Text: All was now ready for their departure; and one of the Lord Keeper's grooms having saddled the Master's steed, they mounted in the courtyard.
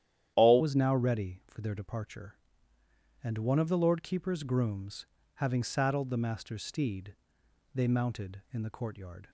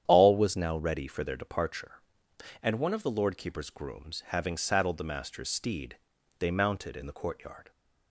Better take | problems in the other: second | starts louder than the rest; strong; until 1.3 s; 11 dB; strong in the second // changes voice at "was"; from 0.5 s on; 8.7 s long // pauses between "grooms" and "having"; slight; at 5.0 s; 0.30 s long

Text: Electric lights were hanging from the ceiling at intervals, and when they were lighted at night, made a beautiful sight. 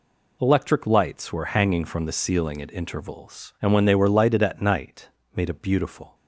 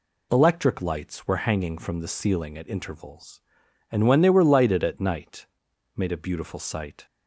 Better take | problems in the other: second | stops before "sight"; at 6.1 s

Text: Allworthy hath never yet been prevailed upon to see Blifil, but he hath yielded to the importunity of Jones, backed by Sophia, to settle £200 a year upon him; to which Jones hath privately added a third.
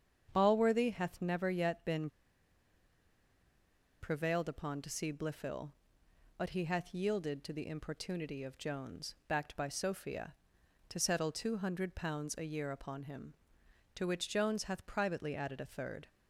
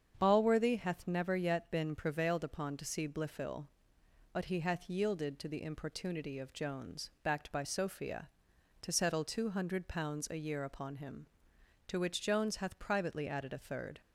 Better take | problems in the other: second | starts louder than the rest; strong; until 1.3 s; 7.5 dB; strong in the second // pauses between "been" and "prevailed"; strong; at 2.0 s; 1.9 s long

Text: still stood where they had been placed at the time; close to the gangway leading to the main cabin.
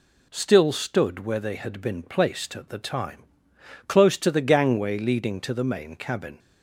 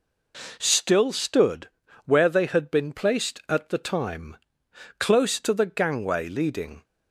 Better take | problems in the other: first | pauses between "stood" and "where"; slight; at 1.6 s; 0.34 s long // stops before "to the main cabin"; at 6.8 s

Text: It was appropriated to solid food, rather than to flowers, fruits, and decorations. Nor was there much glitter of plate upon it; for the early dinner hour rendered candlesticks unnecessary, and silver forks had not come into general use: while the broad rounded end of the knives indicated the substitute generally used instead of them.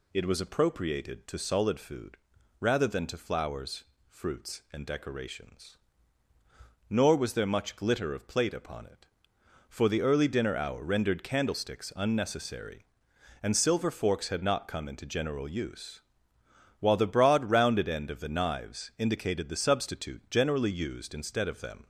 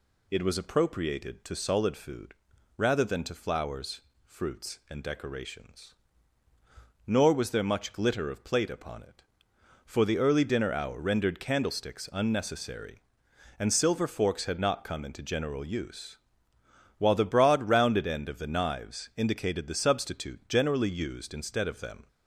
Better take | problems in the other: neither | none

